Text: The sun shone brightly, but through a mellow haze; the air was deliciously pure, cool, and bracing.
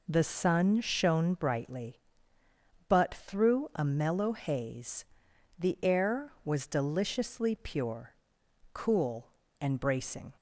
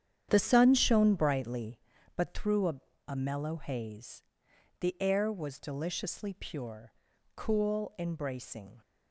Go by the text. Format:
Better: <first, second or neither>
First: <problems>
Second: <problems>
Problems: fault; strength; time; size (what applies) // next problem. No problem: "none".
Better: first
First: none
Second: starts louder than the rest; strong; until 1.3 s; 9 dB // says "a" twice; at 3.0 s